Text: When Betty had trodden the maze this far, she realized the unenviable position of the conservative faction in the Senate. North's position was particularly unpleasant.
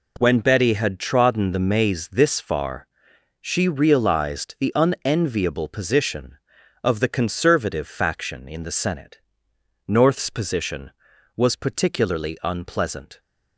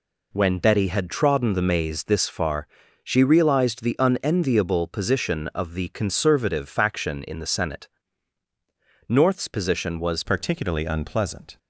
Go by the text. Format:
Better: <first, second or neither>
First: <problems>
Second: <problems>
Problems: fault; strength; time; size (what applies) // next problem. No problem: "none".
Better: first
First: none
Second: changes voice at "particularly"; from 10.2 s on; 1.3 s long